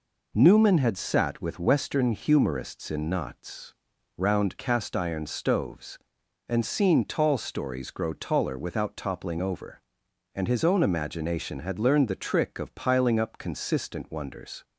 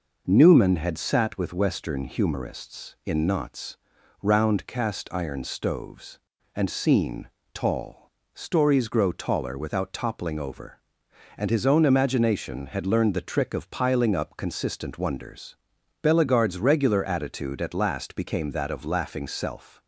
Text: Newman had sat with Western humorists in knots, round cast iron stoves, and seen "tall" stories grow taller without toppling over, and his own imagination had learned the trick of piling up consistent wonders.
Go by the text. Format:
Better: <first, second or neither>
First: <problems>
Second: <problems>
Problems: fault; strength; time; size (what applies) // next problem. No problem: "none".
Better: first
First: none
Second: pauses between "seen" and "tall"; slight; at 7.2 s; 0.24 s long // pauses between "tall" and "stories"; slight; at 8.1 s; 0.22 s long // goes on to say "Bellegarde's regular attitude at last became that of laughing self"; strong; from 16.0 s on; 3.8 s long